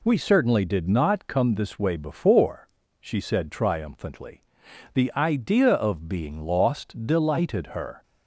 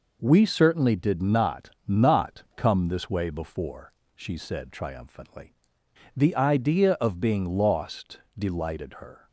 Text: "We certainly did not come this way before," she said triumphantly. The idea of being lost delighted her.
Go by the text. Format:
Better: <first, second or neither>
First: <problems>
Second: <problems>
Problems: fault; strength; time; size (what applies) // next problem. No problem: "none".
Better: first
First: none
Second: says "not" twice; at 1.8 s // pauses between "lost" and "delighted"; slight; at 8.1 s; 0.18 s long